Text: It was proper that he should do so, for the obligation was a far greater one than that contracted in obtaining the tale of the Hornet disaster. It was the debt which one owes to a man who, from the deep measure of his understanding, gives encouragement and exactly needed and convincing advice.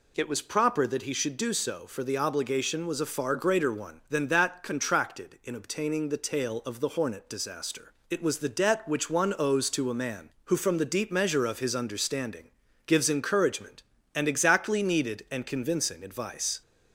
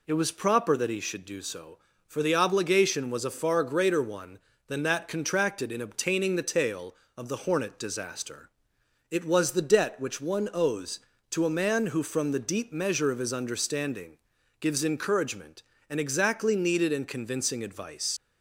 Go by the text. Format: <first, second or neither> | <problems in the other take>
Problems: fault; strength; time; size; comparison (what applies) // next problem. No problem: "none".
first | leaves "advice" unfinished; at 18.1 s; 75 ms